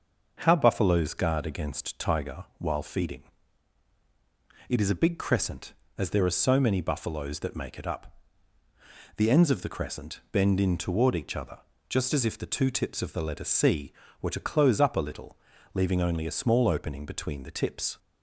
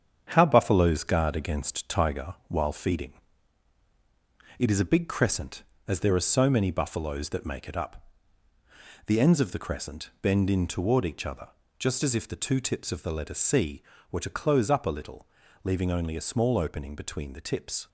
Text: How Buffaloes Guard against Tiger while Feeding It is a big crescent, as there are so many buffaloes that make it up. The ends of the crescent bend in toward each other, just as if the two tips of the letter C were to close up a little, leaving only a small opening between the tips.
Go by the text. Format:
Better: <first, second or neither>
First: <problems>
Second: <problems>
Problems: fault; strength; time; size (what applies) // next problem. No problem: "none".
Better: first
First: starts louder than the rest; until 1.4 s; 6 dB // pauses between "Feeding" and "It"; strong; at 3.2 s; 1.4 s long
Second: gets quieter; noticeable; throughout; 6 dB // starts louder than the rest; strong; until 1.3 s; 8 dB // pauses between "Feeding" and "It"; strong; at 3.1 s; 1.4 s long